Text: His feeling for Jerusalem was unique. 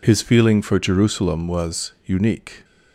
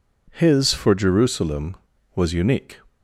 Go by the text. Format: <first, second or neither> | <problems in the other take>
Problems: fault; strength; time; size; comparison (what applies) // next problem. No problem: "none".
first | skips "feeling"; at 0.7 s